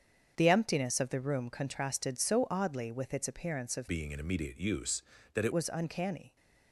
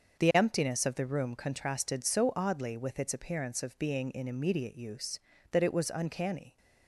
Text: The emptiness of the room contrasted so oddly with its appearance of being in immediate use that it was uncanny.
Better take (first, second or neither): second